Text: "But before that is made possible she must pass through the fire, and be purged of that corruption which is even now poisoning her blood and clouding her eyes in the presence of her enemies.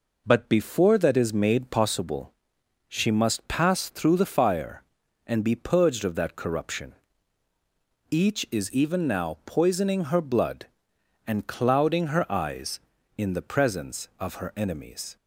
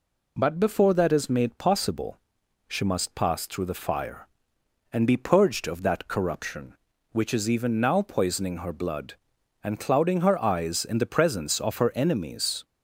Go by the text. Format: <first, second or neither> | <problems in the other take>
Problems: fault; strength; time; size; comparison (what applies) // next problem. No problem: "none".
second | pauses between "possible" and "she"; noticeable; at 2.3 s; 0.54 s long; noticeable in the second // says "each" for "which"; at 8.0 s